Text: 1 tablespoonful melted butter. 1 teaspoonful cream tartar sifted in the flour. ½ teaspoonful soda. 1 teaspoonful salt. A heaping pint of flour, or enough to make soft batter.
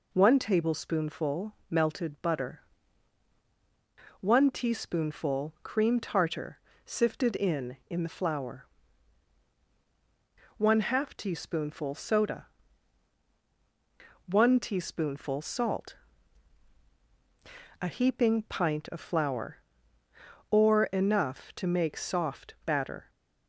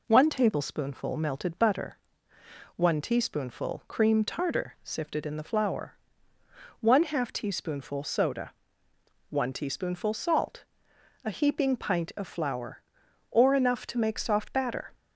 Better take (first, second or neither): second